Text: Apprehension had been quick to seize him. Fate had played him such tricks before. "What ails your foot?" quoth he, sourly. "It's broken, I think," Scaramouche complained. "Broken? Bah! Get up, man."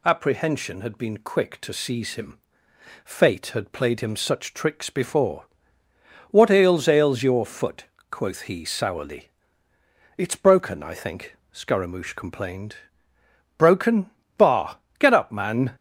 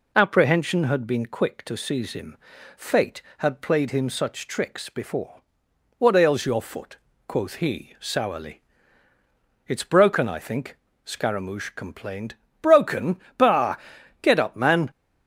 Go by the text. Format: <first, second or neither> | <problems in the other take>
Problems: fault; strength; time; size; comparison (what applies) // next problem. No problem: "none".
second | says "ails" twice; at 6.8 s